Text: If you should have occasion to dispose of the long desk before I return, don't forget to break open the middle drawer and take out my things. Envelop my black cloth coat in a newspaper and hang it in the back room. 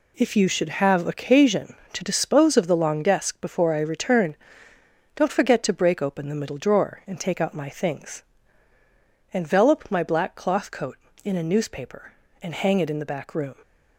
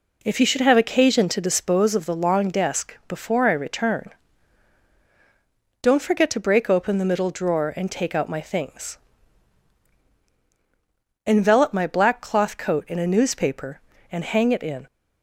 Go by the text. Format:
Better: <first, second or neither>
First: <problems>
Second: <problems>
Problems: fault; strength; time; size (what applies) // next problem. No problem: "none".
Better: first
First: none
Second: stops before "the back room"; at 14.8 s